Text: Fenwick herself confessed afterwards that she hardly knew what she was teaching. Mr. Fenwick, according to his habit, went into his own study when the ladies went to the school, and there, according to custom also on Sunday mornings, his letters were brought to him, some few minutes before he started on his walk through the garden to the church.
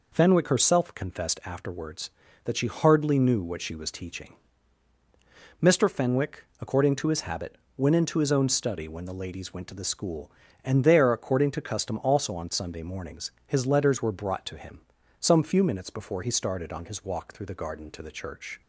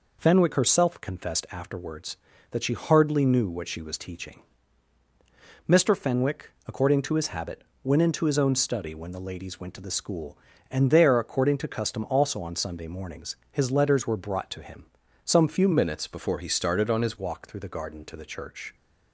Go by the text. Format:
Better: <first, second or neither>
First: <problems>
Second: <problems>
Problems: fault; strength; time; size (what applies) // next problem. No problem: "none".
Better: first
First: none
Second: changes voice from "minutes" to "his"; from 15.7 to 17.1 s; 1.4 s long